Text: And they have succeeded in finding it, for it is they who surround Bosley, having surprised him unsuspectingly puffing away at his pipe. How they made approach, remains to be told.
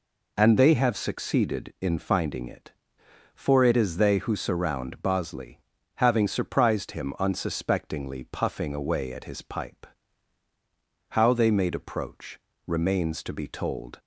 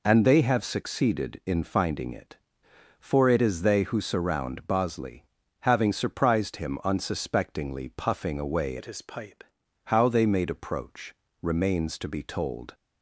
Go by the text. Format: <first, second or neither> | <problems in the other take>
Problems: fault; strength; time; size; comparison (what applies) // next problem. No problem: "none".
first | changes voice from "at" to "pipe"; from 8.7 to 9.4 s; 0.7 s long